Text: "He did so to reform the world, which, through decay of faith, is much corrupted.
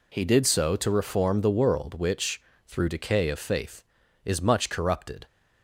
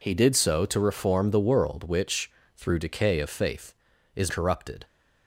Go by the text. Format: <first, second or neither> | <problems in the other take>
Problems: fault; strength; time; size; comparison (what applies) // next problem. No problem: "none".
first | skips "much"; at 4.3 s